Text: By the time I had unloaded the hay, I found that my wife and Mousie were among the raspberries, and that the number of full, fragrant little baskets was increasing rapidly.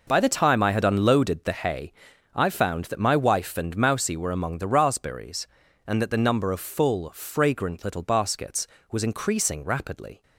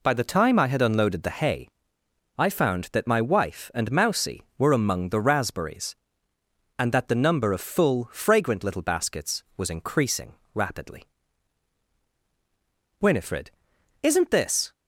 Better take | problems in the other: first | pauses between "increasing" and "rapidly"; slight; at 10.3 s; 0.18 s long // goes on to say "Winifred isn't this"; strong; from 12.9 s on; 1.7 s long

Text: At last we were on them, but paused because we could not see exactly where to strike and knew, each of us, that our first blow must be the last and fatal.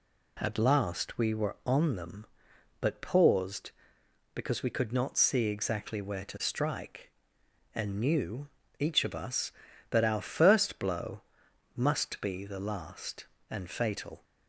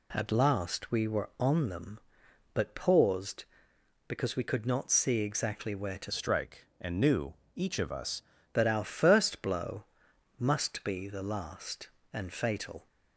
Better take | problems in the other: first | changes voice from "strike" to "us"; from 6.1 to 8.2 s; 2.1 s long // pauses between "blow" and "must"; noticeable; at 9.8 s; 0.54 s long; noticeable in the first

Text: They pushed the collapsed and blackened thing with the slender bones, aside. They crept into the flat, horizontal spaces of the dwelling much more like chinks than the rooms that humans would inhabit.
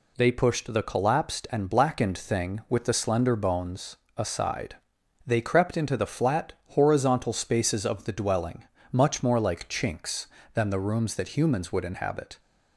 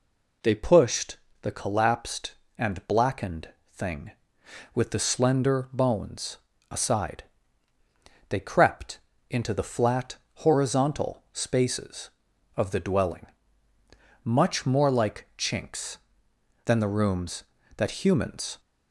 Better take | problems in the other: first | pauses between "pushed" and "the"; slight; at 1.1 s; 0.24 s long // pauses between "blackened" and "thing"; slight; at 3.4 s; 0.22 s long // pauses between "crept" and "into"; slight; at 8.9 s; 0.28 s long // pauses between "dwelling" and "much"; noticeable; at 13.2 s; 0.98 s long; slight in the first // stops before "would inhabit"; at 18.5 s

